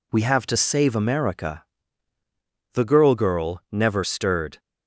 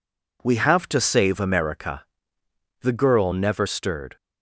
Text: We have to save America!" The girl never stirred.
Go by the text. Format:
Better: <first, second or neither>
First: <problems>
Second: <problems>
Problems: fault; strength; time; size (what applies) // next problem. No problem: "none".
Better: second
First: says "girl" twice; at 3.1 s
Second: none